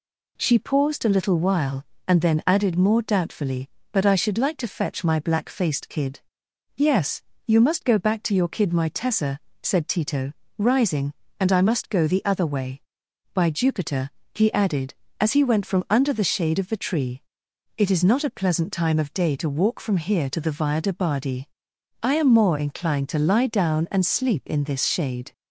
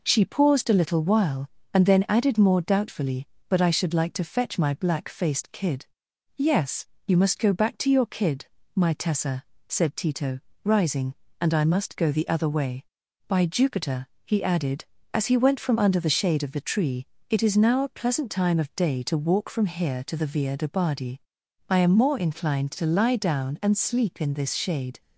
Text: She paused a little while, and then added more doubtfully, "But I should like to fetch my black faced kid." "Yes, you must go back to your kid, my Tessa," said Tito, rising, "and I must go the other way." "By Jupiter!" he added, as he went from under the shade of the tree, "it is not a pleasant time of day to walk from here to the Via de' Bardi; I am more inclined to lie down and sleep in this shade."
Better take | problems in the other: first | says "now" for "not"; at 17.5 s

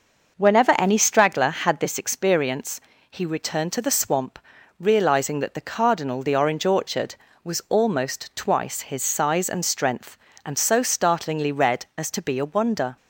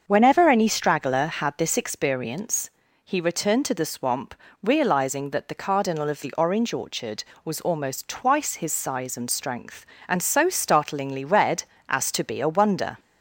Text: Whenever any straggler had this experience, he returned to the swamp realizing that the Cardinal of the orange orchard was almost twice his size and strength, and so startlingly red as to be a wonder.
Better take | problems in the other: second | starts louder than the rest; noticeable; until 1.4 s; 6 dB; also in the second // pauses between "swamp" and "realizing"; at 4.3 s; 0.40 s long; slight in the second // skips "of"; at 6.2 s

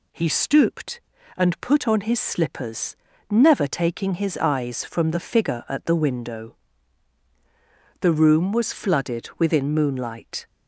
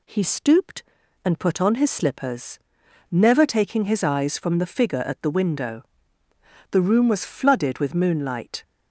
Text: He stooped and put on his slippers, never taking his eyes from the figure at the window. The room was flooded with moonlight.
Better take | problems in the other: second | says "within" for "with"; at 9.3 s

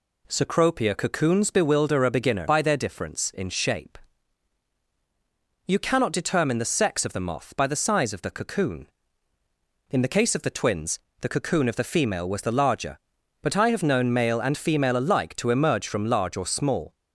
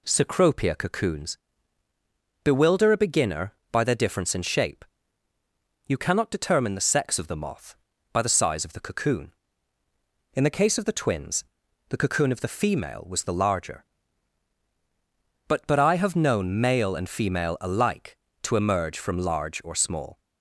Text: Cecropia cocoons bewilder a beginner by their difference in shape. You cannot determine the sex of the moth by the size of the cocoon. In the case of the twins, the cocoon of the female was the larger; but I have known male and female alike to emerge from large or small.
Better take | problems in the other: first | pauses between "cocoons" and "bewilder"; at 1.3 s; 1.0 s long // says "but" twice; at 15.6 s

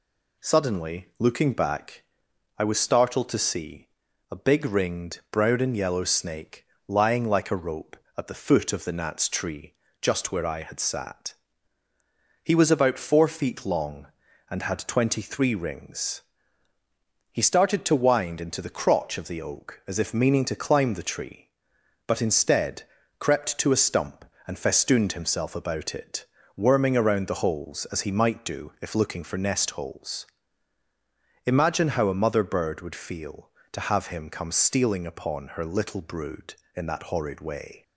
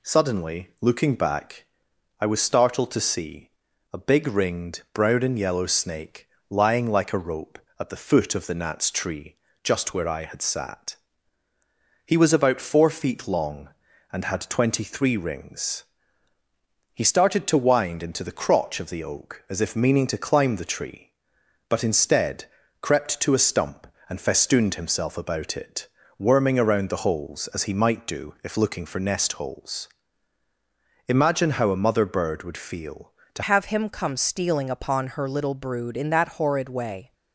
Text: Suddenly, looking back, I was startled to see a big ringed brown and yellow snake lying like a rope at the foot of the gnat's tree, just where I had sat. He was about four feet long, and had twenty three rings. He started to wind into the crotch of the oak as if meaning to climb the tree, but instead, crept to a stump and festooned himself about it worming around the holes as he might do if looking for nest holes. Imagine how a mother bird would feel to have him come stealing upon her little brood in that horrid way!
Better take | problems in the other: first | pauses between "see" and "a"; at 3.5 s; 0.42 s long; also in the first // pauses between "snake" and "lying"; slight; at 6.2 s; 0.22 s long; slight in the first // pauses between "it" and "worming"; slight; at 25.8 s; 0.30 s long; slight in the first // changes voice at "have"; from 33.4 s on; 3.7 s long

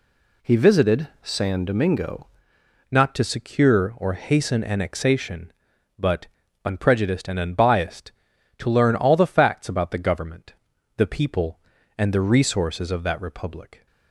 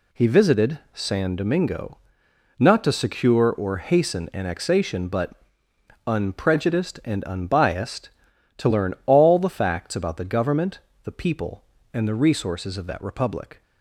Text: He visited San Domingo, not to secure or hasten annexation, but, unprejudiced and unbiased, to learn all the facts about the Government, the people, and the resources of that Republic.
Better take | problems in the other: second | changes voice at "not"; from 2.9 s on; 10.9 s long

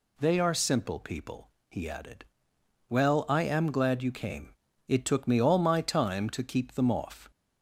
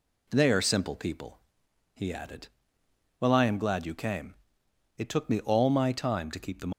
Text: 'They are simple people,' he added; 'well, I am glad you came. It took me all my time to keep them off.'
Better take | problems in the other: first | stops before "off"; at 6.7 s

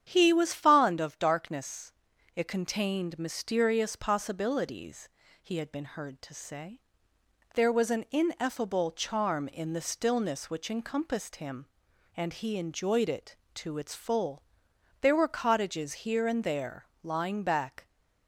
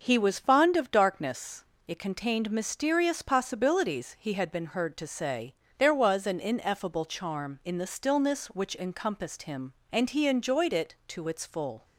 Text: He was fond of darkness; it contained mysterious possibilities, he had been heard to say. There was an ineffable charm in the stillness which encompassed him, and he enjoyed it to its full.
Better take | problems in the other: second | starts louder than the rest; strong; until 1.1 s; 9 dB; also in the second // goes on to say "There were cottages here and there lying back"; strong; from 15.0 s on; 2.8 s long

